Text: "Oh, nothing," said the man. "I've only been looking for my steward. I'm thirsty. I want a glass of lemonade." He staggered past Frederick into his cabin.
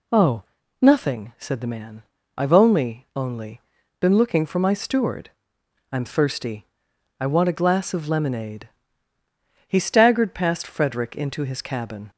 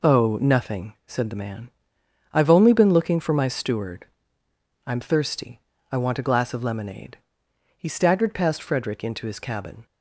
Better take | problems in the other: second | says "only" twice; at 3.1 s

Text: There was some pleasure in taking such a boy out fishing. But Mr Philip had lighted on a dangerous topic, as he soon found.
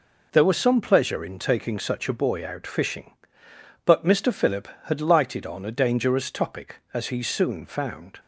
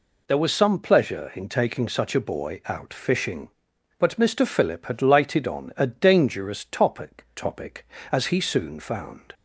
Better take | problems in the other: first | says "topic" twice; at 7.3 s

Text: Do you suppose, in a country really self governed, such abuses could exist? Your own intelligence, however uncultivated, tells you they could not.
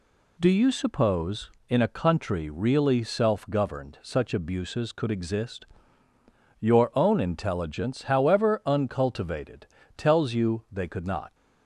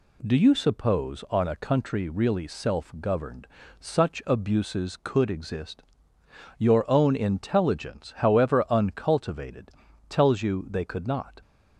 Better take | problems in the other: first | says "on" for "in"; at 1.3 s

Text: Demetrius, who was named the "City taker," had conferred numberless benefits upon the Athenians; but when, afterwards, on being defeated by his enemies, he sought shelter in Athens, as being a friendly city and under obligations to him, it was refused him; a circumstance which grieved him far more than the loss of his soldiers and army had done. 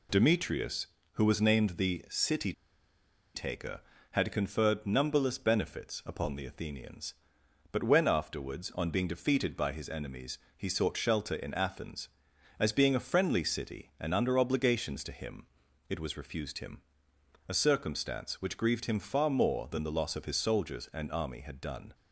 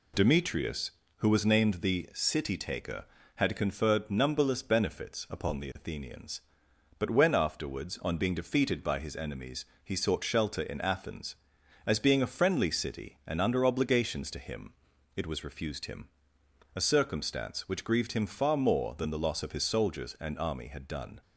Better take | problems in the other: second | pauses between "City" and "taker"; noticeable; at 2.5 s; 0.82 s long

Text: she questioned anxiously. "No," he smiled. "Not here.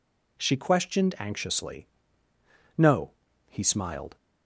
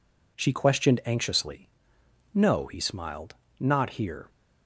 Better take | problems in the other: second | stops before "Not here"; at 4.1 s

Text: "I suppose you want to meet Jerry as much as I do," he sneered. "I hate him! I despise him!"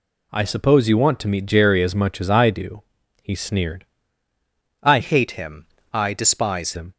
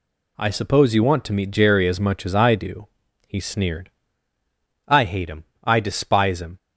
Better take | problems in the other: second | changes voice from "hate" to "despise"; from 4.9 to 6.7 s; 1.8 s long

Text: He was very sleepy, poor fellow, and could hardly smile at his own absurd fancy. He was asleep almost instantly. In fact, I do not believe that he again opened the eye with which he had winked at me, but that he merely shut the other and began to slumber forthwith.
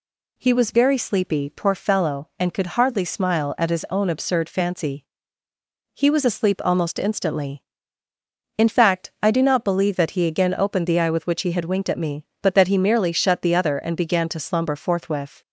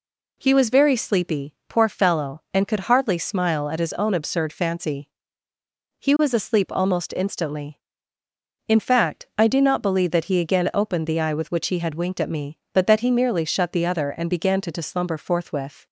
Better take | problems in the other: first | says "to" twice; at 14.7 s

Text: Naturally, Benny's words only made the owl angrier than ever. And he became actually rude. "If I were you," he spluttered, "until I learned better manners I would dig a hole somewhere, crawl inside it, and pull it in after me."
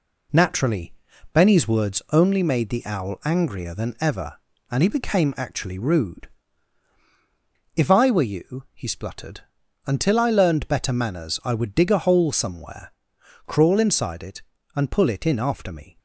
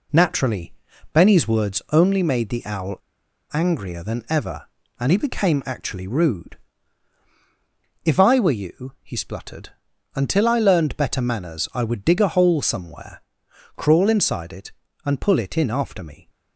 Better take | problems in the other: first | pauses between "owl" and "angrier"; noticeable; at 2.9 s; 0.54 s long

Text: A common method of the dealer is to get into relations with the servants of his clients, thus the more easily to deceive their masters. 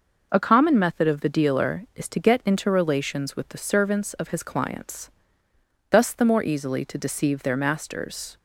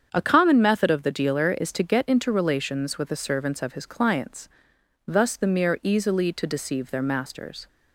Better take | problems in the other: first | starts louder than the rest; strong; until 1.1 s; 7.5 dB // says "mere" for "more"; at 5.4 s

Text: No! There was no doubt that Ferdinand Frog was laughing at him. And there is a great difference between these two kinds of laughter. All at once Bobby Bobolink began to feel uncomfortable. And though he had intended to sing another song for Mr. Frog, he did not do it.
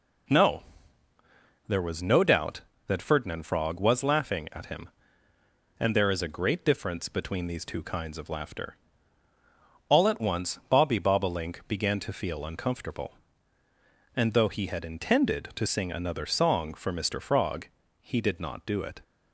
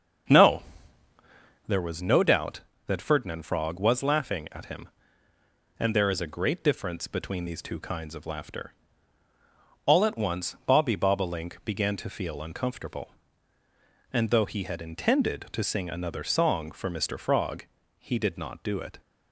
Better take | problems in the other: first | starts louder than the rest; strong; until 1.8 s; 7.5 dB

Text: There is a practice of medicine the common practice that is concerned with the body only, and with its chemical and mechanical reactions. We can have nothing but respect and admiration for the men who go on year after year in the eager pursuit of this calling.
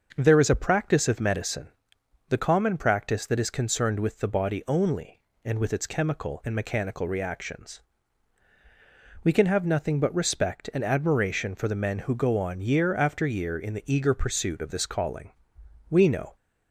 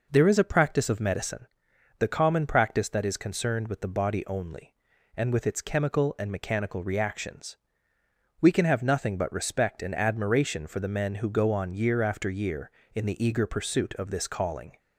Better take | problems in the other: second | starts louder than the rest; until 1.1 s; 6.5 dB // pauses between "medicine" and "the"; noticeable; at 1.6 s; 0.58 s long; noticeable in the second // goes on to say "We know"; slight; from 15.8 s on; 0.46 s long

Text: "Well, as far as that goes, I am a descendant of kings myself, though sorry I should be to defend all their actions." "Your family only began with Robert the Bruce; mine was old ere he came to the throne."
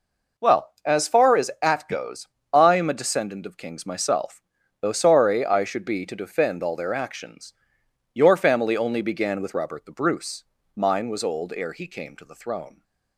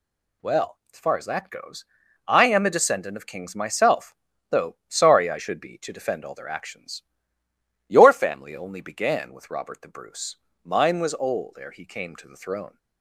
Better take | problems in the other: second | says "at" for "that"; at 1.6 s

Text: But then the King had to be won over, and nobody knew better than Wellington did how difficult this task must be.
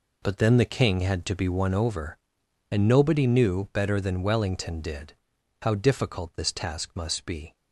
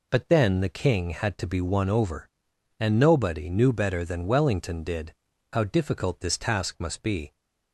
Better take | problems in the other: second | gets quieter; strong; throughout; 11 dB // pauses between "did" and "how"; noticeable; at 5.1 s; 0.48 s long; also in the second

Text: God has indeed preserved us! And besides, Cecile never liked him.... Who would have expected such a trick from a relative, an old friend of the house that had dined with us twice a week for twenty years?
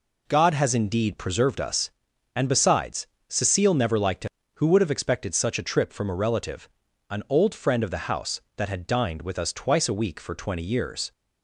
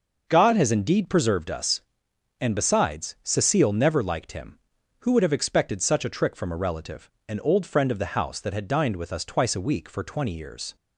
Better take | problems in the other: second | says "trip" for "trick"; at 5.6 s

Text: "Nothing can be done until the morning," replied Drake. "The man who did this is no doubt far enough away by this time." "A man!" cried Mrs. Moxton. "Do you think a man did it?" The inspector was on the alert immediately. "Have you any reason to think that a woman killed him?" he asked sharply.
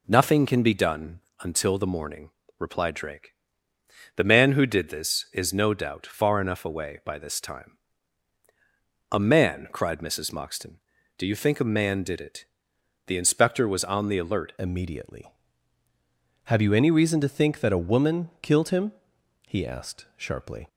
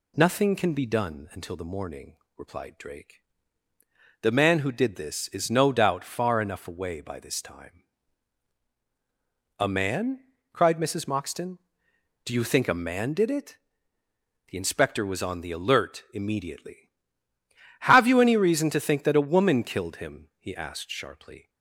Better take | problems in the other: second | pauses between "done" and "until"; slight; at 1.2 s; 0.20 s long // changes voice at "immediately"; from 14.5 s on; 6.1 s long

